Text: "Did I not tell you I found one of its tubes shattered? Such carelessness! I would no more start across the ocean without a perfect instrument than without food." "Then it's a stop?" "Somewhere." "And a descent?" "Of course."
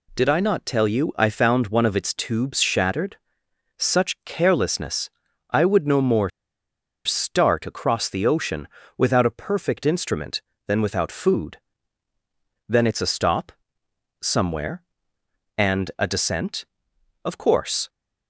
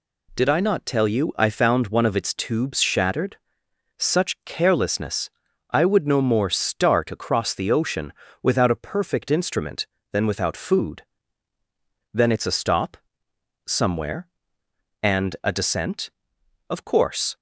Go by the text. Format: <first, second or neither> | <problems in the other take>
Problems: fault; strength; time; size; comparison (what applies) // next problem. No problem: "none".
second | pauses between "more" and "start"; noticeable; at 6.2 s; 0.75 s long // pauses between "ocean" and "without"; slight; at 8.6 s; 0.30 s long; slight in the second